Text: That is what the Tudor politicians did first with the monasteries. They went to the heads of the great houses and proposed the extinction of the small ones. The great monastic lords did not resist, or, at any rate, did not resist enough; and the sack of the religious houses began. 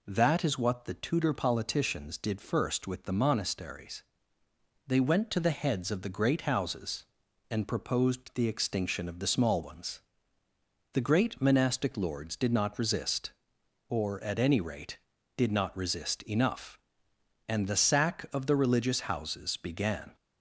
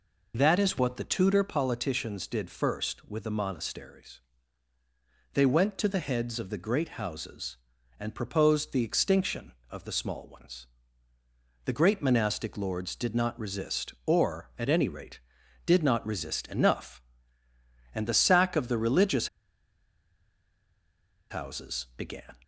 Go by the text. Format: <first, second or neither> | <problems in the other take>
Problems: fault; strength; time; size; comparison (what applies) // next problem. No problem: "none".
first | pauses between "religious" and "houses"; strong; at 19.2 s; 2.0 s long